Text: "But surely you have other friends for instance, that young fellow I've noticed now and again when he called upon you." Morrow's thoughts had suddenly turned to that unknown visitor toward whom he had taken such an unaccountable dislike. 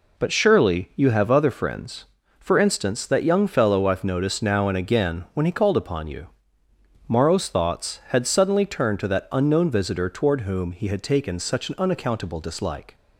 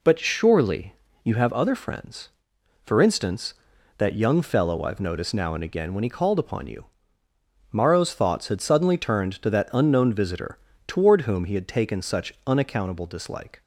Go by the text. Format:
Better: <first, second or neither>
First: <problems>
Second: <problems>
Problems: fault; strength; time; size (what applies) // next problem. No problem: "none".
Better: first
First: none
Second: pauses between "surely" and "you"; slight; at 0.9 s; 0.28 s long // pauses between "visitor" and "toward"; slight; at 10.5 s; 0.30 s long // skips "an"; at 12.3 s